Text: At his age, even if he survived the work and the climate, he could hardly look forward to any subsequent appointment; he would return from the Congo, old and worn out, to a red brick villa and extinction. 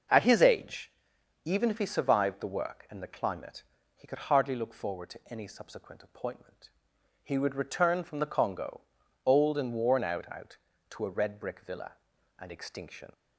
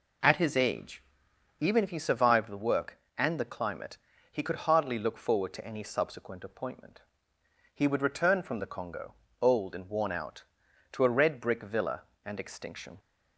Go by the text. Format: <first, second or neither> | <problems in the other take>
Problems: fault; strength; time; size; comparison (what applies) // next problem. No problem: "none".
second | says "out" twice; at 10.3 s